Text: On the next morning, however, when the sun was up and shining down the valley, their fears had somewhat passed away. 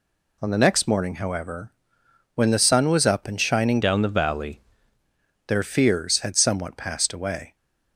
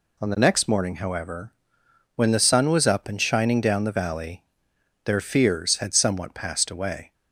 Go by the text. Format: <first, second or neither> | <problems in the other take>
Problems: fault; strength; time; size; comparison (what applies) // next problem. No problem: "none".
second | changes voice from "down" to "valley"; from 3.8 to 4.6 s; 0.8 s long